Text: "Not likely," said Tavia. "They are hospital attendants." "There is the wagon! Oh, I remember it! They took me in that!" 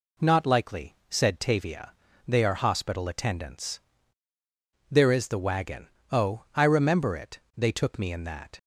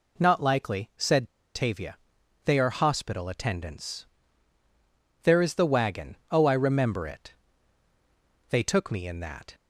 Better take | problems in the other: first | pauses between "said" and "Tavia"; slight; at 1.2 s; 0.27 s long

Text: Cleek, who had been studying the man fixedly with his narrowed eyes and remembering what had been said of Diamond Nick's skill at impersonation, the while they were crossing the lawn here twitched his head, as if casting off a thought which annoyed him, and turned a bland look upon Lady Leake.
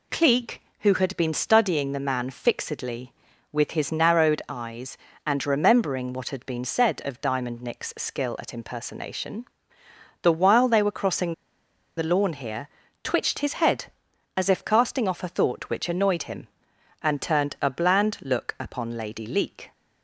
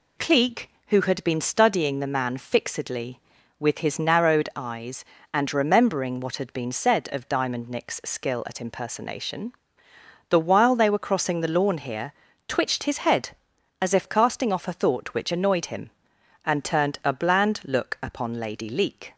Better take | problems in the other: second | pauses between "crossing" and "the"; noticeable; at 11.3 s; 0.64 s long // pauses between "here" and "twitched"; slight; at 12.6 s; 0.36 s long; slight in the second

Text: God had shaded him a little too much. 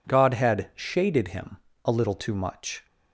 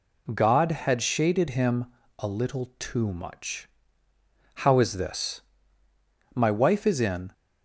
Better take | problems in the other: first | pauses between "him" and "a"; slight; at 1.8 s; 0.34 s long; slight in the first // goes on to say "How is this my wife is in"; strong; from 4.5 s on; 2.7 s long

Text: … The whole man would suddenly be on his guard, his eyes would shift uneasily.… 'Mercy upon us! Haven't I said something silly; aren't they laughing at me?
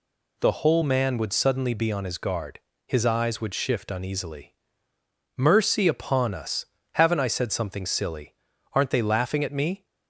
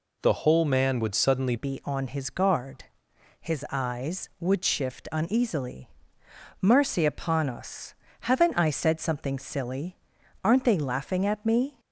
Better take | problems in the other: first | changes voice at "be"; from 1.5 s on; 10.2 s long

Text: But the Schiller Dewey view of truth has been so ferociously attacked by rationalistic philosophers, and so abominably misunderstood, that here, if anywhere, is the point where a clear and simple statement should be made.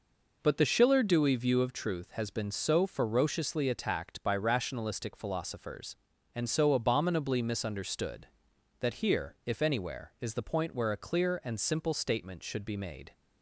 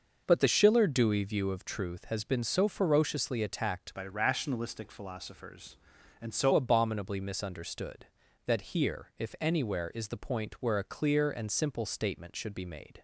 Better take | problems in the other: first | starts louder than the rest; noticeable; until 1.2 s; 6 dB // changes voice from "by" to "so"; from 3.9 to 6.5 s; 2.6 s long

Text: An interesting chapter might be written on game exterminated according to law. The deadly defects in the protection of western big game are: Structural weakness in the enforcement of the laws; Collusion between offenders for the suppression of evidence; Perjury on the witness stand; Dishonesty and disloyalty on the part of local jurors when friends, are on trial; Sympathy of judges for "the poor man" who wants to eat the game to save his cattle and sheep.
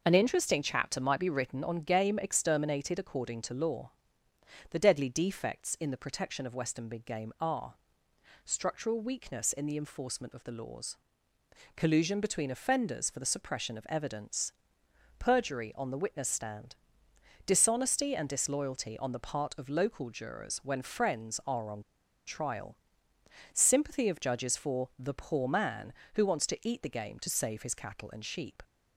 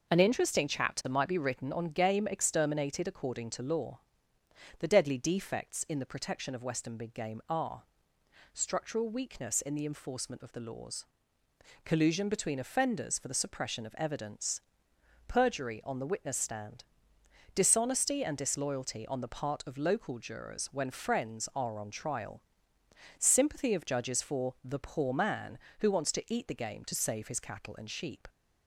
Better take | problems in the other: second | pauses between "on" and "trial"; at 21.8 s; 0.45 s long

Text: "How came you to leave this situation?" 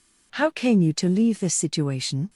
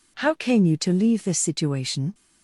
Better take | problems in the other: neither | none

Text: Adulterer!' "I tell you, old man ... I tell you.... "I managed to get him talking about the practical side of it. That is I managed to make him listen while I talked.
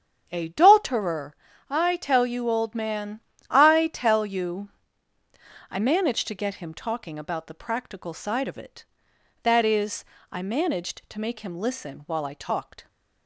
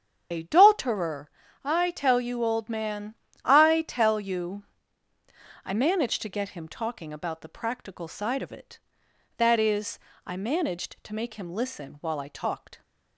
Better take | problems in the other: first | loses the start of "Adulterer"; at 0.3 s; 70 ms // starts louder than the rest; strong; until 1.6 s; 8 dB; strong in the first // pauses between "is" and "I"; slight; at 9.9 s; 0.26 s long; slight in the first

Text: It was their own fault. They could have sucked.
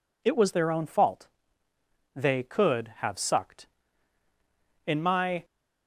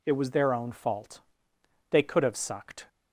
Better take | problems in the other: second | goes on to say "In my"; from 4.8 s on; 0.58 s long

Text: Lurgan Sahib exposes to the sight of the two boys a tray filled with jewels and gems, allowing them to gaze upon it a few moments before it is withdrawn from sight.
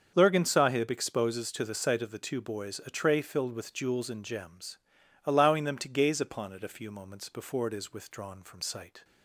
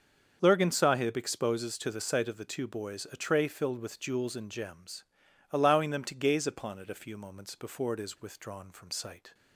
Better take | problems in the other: neither | starts louder than the rest; the same in both

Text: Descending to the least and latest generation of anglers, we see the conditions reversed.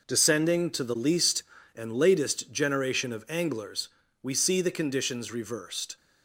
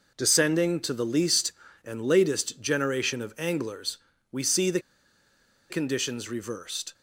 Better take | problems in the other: first | pauses between "the" and "conditions"; noticeable; at 4.7 s; 0.90 s long

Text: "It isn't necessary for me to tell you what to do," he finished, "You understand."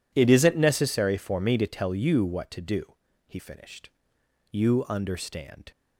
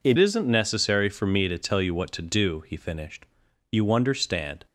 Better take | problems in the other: first | changes voice at "isn't"; from 0.1 s on; 4.5 s long

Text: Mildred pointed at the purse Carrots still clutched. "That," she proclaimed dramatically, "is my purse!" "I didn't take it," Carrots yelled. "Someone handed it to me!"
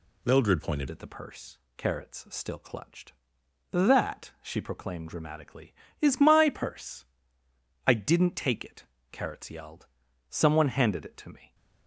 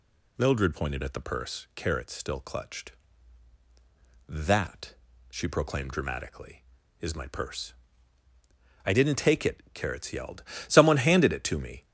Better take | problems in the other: second | changes voice at "at"; from 0.8 s on; 10.7 s long // pauses between "purse" and "Carrots"; slight; at 1.5 s; 0.18 s long

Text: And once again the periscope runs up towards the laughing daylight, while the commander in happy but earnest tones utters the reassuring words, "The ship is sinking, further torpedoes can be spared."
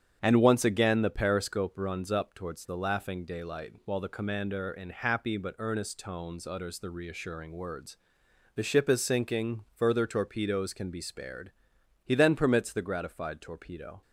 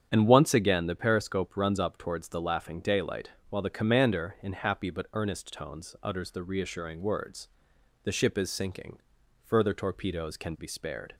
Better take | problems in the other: second | starts louder than the rest; strong; until 1.2 s; 8 dB; strong in the second // goes on to say "He then permits the gratified torpedo"; strong; from 12.0 s on; 1.9 s long

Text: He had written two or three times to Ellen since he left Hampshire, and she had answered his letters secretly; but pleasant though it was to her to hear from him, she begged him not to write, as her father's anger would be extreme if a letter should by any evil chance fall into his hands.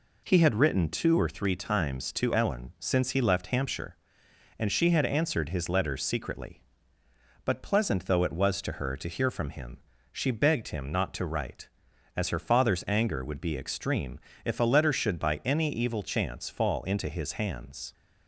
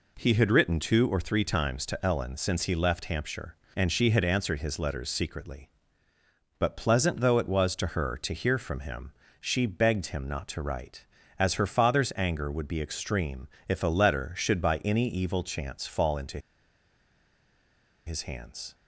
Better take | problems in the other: first | pauses between "extreme" and "if"; slight; at 13.4 s; 0.18 s long; slight in the first // pauses between "into" and "his"; strong; at 16.3 s; 1.6 s long

